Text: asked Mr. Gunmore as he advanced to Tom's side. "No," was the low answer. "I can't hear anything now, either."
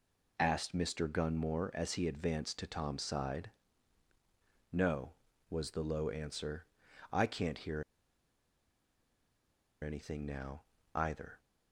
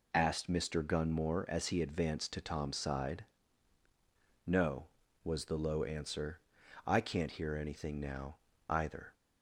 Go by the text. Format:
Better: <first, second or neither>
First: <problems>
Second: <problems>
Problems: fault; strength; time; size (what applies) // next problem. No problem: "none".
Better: second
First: pauses between "hear" and "anything"; strong; at 7.8 s; 1.9 s long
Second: none